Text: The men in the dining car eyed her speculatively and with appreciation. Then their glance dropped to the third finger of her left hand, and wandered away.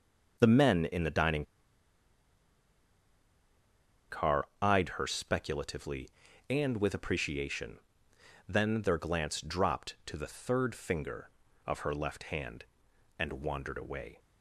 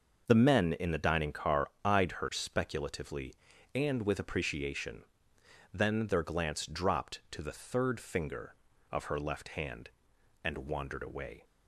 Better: second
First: pauses between "dining" and "car"; strong; at 1.4 s; 2.6 s long // pauses between "car" and "eyed"; slight; at 4.4 s; 0.16 s long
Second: pauses between "car" and "eyed"; slight; at 1.6 s; 0.16 s long

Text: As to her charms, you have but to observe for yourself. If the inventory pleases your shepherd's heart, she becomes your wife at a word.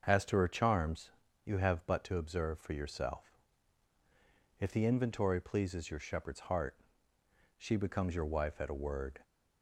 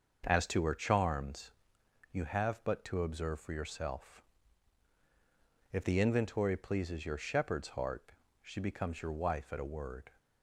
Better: neither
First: starts louder than the rest; until 1.0 s; 6.5 dB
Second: starts louder than the rest; until 1.2 s; 6.5 dB

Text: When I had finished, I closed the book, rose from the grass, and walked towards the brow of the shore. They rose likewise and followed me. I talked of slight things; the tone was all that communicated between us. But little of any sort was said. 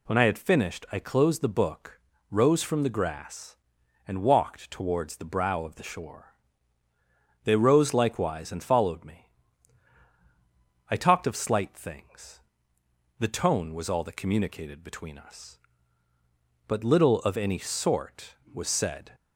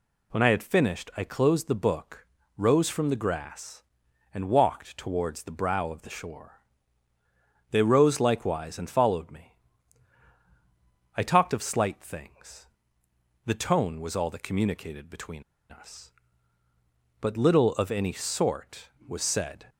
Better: first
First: none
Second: pauses between "between" and "us"; slight; at 15.4 s; 0.26 s long

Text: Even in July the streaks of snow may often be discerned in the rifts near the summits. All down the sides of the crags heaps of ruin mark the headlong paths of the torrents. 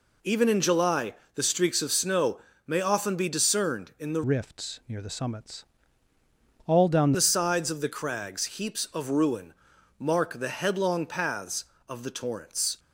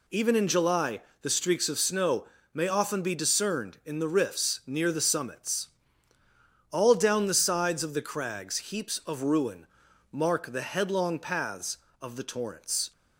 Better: second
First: pauses between "July" and "the"; slight; at 1.1 s; 0.20 s long // pauses between "snow" and "may"; slight; at 2.3 s; 0.28 s long // changes voice from "rifts" to "down"; from 4.2 to 7.1 s; 2.9 s long // pauses between "ruin" and "mark"; noticeable; at 9.5 s; 0.46 s long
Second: pauses between "July" and "the"; slight; at 1.0 s; 0.20 s long // pauses between "snow" and "may"; slight; at 2.2 s; 0.28 s long // pauses between "ruin" and "mark"; noticeable; at 9.6 s; 0.46 s long

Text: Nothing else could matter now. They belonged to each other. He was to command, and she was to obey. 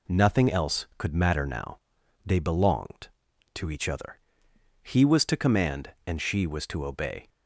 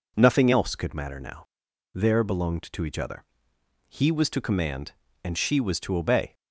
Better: first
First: none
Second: says "There" for "They"; at 1.9 s

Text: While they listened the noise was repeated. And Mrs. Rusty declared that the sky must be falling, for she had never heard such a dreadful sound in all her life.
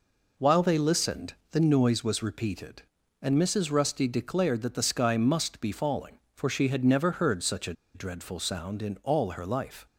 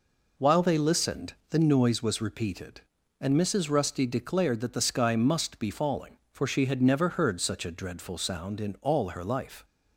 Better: second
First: pauses between "listened" and "the"; slight; at 1.3 s; 0.20 s long // pauses between "a" and "dreadful"; slight; at 7.7 s; 0.21 s long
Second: pauses between "listened" and "the"; slight; at 1.3 s; 0.18 s long

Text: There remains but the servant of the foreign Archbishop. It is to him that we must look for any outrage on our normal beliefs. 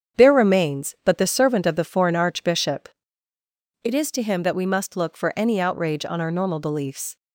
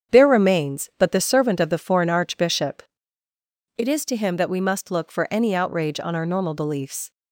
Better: neither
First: starts louder than the rest; strong; until 1.2 s; 8 dB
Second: starts louder than the rest; strong; until 1.1 s; 8 dB

